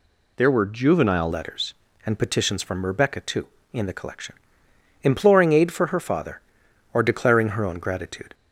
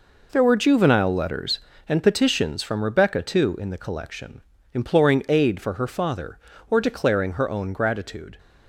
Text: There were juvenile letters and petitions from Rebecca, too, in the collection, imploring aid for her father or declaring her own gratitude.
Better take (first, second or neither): second